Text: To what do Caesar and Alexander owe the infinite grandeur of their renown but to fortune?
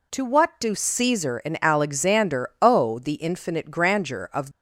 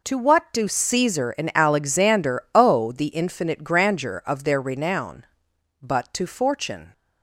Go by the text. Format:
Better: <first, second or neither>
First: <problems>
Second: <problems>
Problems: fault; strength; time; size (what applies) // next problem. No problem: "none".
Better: second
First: stops before "their renown but to fortune"; at 4.5 s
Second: none